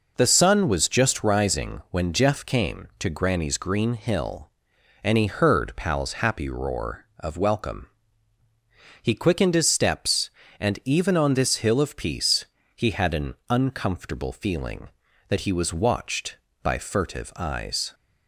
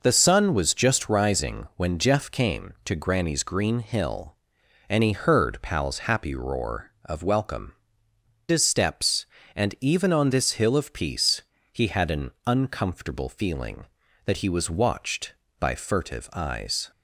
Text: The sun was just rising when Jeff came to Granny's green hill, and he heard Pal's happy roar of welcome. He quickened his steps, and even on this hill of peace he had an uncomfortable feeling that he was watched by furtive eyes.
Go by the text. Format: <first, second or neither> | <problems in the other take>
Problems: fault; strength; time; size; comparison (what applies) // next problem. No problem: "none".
first | skips "He quickened"; at 8.1 s // pauses between "peace" and "he"; slight; at 11.4 s; 0.32 s long; slight in the first